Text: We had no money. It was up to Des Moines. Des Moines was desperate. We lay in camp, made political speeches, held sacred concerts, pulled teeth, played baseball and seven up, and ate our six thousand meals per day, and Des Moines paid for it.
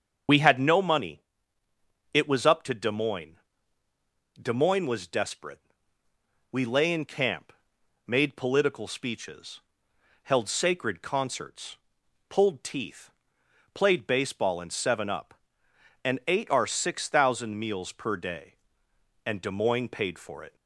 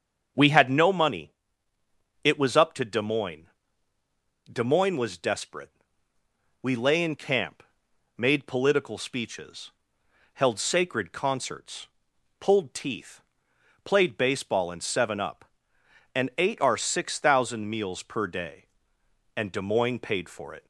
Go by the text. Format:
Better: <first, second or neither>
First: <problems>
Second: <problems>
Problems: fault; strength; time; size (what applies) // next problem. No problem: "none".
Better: second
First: loses the start of "We"; at 0.2 s; 30 ms // starts louder than the rest; strong; until 2.1 s; 7 dB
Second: starts louder than the rest; until 2.2 s; 7 dB